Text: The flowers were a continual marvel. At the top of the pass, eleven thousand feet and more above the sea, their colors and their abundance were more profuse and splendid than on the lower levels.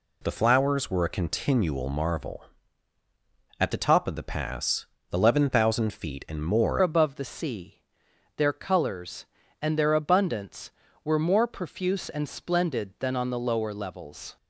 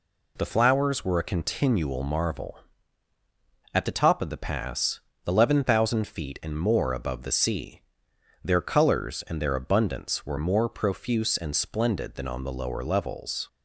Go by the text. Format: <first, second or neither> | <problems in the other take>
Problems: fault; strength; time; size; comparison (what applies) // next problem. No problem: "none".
second | changes voice at "above"; from 6.8 s on; 7.5 s long